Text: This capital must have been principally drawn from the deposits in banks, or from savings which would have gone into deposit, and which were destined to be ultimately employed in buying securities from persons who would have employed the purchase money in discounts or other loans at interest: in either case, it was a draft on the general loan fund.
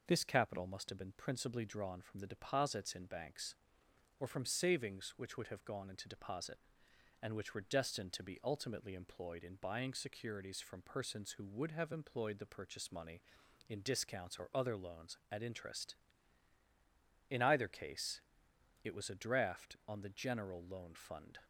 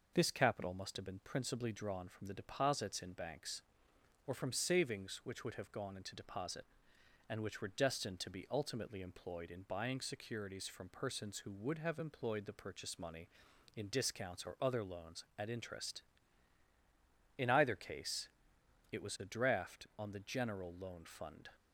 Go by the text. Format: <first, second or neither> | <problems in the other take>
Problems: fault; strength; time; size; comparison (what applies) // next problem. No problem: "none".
neither | none